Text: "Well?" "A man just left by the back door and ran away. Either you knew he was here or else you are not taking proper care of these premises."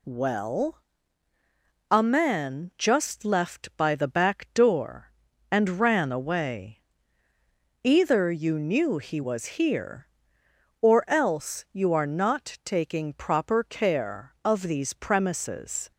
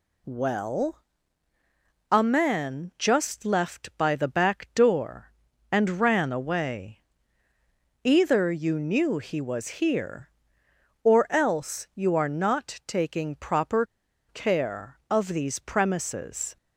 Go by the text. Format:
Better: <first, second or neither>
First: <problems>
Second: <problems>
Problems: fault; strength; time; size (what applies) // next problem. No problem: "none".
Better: first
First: pauses between "was" and "here"; slight; at 9.4 s; 0.16 s long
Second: pauses between "was" and "here"; slight; at 9.6 s; 0.16 s long // pauses between "proper" and "care"; at 13.8 s; 0.44 s long